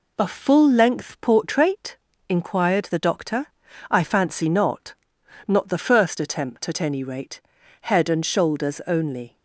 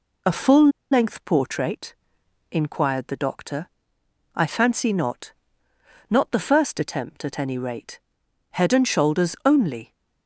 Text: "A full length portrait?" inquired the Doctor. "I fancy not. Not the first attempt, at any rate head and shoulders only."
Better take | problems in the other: first | pauses between "full" and "length"; slight; at 0.6 s; 0.22 s long // pauses between "rate" and "head"; noticeable; at 7.9 s; 0.54 s long; also in the first

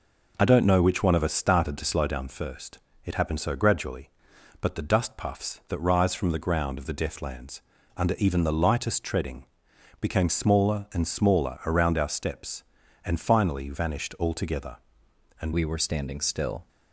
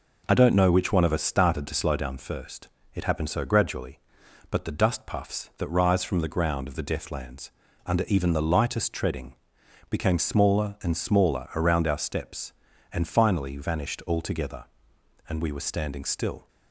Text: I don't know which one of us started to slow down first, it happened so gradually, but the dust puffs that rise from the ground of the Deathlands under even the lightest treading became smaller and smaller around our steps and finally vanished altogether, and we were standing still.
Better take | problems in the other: second | pauses between "Deathlands" and "under"; slight; at 7.6 s; 0.34 s long; slight in the second // pauses between "treading" and "became"; noticeable; at 9.4 s; 0.56 s long; noticeable in the second // changes voice at "we"; from 15.5 s on; 1.1 s long

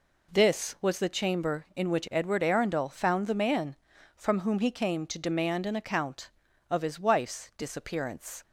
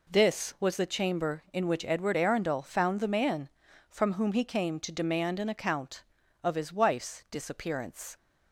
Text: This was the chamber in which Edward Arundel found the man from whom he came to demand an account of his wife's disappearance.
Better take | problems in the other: neither | none

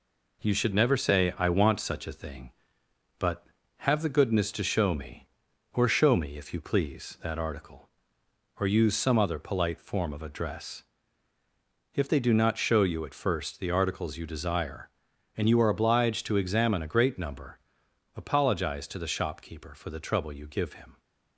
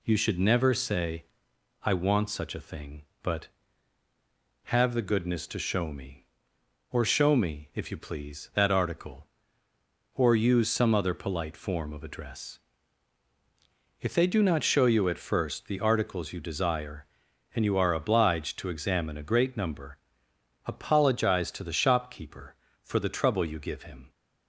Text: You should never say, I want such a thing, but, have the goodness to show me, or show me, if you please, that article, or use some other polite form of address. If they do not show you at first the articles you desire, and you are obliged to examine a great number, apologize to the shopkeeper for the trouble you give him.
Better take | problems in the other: second | gets quieter; noticeable; throughout; 4.5 dB

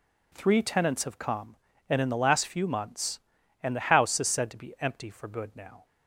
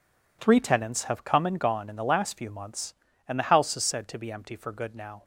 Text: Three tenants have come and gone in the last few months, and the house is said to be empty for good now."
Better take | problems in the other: second | skips "gone"; at 2.0 s

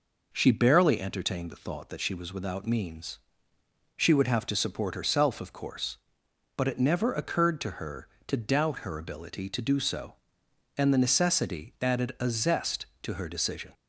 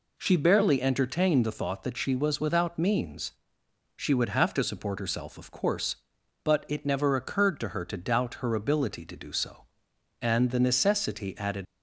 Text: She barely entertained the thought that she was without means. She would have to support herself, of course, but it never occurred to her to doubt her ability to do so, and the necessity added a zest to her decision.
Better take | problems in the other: first | stops before "a zest to her decision"; at 11.6 s

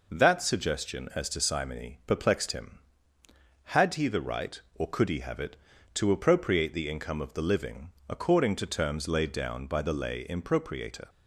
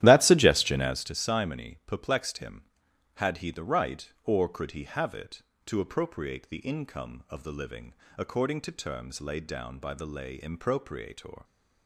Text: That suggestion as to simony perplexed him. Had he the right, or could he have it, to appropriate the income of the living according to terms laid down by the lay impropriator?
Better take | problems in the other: first | starts louder than the rest; strong; until 1.1 s; 13 dB // pauses between "living" and "according"; slight; at 7.9 s; 0.24 s long; slight in the first

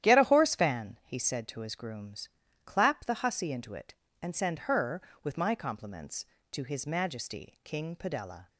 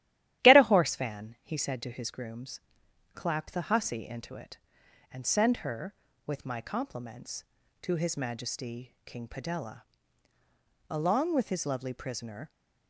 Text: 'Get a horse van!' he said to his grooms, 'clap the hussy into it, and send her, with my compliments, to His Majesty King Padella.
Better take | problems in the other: first | starts louder than the rest; strong; until 1.4 s; 13 dB; strong in the first // goes on to say "Along with his lovely prisoner"; from 10.8 s on; 1.6 s long

